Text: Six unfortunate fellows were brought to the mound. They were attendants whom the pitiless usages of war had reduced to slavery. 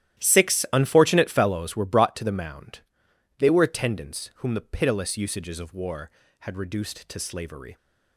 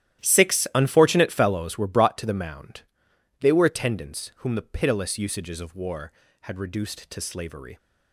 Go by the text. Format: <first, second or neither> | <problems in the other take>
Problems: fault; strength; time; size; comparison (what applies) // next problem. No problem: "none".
neither | starts louder than the rest; strong; the same in both